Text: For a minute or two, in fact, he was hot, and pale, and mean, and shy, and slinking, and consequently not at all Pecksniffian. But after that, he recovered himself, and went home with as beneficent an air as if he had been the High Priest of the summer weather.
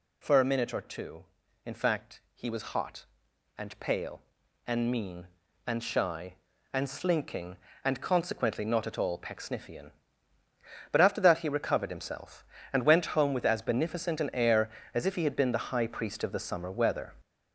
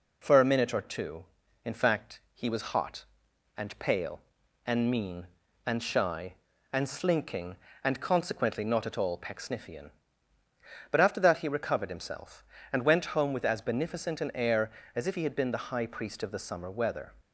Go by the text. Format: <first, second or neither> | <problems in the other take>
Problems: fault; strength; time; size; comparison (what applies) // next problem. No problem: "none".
second | gets louder; noticeable; throughout; 6 dB